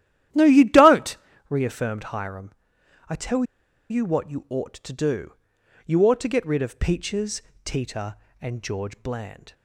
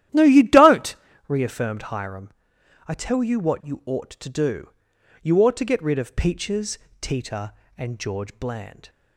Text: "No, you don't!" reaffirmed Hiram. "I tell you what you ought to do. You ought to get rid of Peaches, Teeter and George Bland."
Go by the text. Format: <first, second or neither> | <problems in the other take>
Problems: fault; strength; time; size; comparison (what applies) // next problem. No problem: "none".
second | starts louder than the rest; strong; until 1.6 s; 12.5 dB; strong in the second // pauses between "tell" and "you"; noticeable; at 3.4 s; 0.47 s long